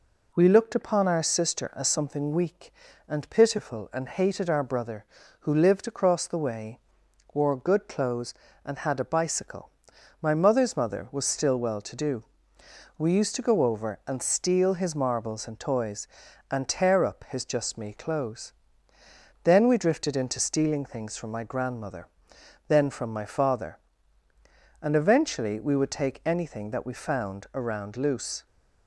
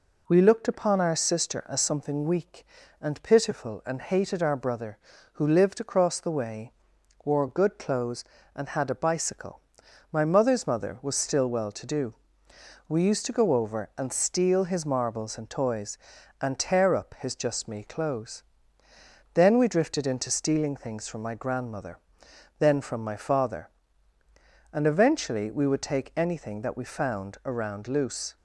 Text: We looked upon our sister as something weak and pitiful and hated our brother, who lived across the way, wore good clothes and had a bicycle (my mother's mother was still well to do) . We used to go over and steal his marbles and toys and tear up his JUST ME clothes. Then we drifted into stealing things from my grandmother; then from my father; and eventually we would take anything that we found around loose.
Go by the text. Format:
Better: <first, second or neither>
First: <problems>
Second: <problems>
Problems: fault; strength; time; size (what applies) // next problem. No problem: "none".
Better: neither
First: none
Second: none